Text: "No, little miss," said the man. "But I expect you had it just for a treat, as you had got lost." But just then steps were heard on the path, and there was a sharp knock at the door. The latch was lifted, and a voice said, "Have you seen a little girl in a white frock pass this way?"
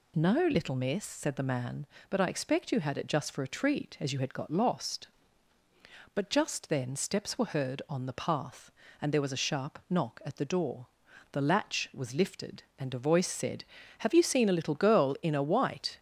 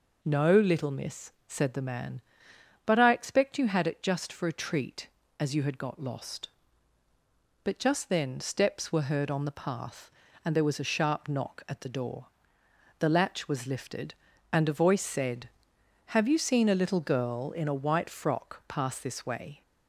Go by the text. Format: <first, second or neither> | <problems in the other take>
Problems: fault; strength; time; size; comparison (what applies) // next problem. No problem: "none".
second | stops before "frock pass this way"; at 15.9 s